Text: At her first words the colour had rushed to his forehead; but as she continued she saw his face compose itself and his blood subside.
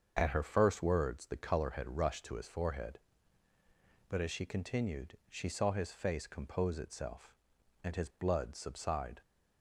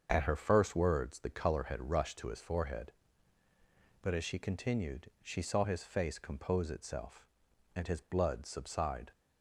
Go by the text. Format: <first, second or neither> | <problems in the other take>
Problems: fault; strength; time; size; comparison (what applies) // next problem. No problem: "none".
neither | starts louder than the rest; the same in both